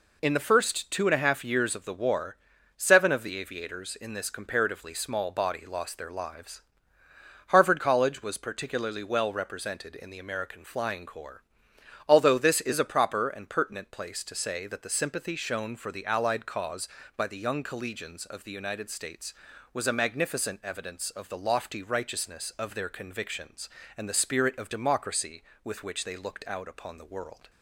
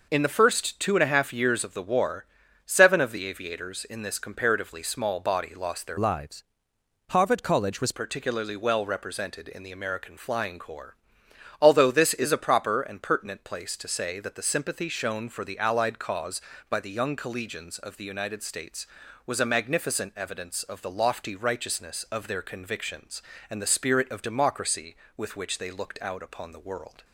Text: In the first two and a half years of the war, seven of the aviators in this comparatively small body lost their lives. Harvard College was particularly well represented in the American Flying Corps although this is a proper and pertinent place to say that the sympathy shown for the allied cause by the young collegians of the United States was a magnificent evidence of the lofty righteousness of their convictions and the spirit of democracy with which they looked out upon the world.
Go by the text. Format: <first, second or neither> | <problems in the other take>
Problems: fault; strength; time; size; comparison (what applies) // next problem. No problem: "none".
first | changes voice from "lives" to "was"; from 5.9 to 7.9 s; 2.0 s long // pauses between "Corps" and "although"; noticeable; at 10.9 s; 0.64 s long; noticeable in the first